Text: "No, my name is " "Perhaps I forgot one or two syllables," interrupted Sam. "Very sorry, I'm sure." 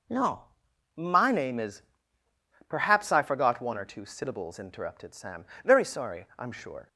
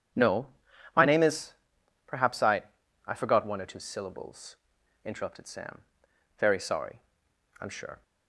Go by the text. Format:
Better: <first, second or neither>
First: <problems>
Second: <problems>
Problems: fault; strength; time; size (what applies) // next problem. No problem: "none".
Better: first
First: none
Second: starts louder than the rest; strong; until 1.8 s; 9 dB // says "I" twice; at 3.0 s